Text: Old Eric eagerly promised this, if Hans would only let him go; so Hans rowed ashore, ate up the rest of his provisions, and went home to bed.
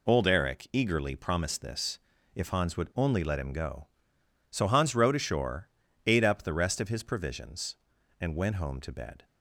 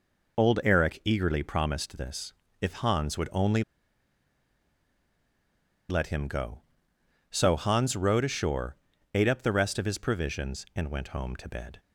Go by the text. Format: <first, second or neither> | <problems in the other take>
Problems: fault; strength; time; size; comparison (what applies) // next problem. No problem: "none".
first | pauses between "only" and "let"; strong; at 3.6 s; 2.2 s long